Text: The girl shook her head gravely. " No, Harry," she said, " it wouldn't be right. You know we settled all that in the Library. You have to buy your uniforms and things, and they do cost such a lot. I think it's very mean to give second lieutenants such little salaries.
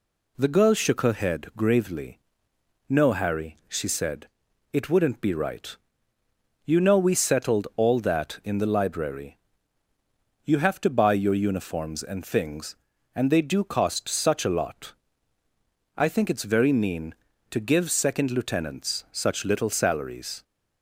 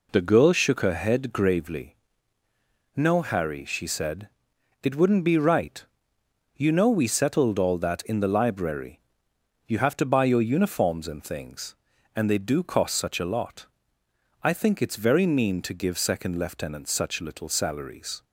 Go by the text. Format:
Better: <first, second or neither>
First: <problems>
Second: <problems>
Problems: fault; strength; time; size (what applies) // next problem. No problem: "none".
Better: neither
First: none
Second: none